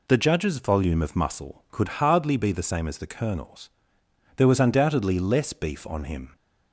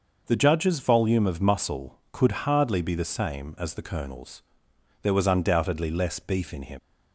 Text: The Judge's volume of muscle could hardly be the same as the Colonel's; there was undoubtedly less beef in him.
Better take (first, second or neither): second